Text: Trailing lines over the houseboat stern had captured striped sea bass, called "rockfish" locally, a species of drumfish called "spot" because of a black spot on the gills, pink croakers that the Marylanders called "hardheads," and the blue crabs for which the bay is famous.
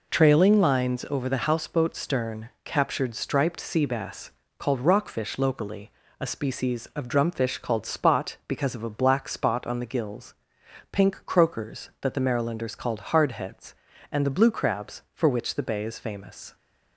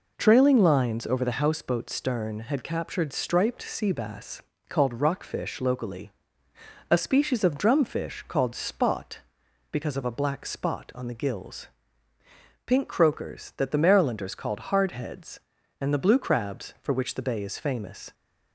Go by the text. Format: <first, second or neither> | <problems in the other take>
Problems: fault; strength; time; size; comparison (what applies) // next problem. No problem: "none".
second | skips "had"; at 2.5 s